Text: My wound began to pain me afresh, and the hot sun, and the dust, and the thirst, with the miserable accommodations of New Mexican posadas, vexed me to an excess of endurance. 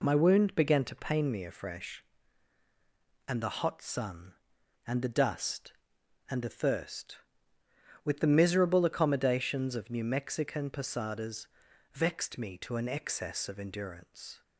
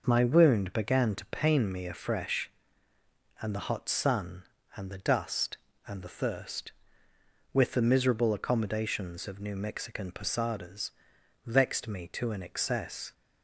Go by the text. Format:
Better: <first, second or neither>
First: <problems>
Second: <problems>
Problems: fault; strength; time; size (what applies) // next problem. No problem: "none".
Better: first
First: none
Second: stops before "of endurance"; at 13.1 s